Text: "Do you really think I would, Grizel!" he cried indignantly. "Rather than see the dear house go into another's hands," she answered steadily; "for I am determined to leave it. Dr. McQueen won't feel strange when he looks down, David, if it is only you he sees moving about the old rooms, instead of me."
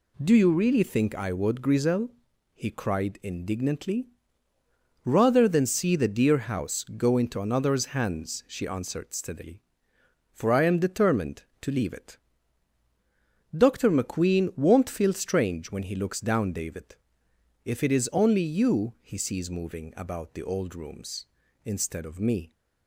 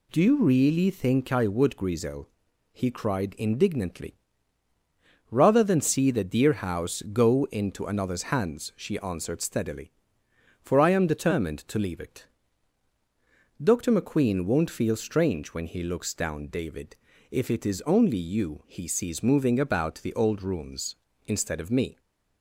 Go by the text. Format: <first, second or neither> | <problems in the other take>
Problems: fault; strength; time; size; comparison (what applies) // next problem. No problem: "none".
neither | none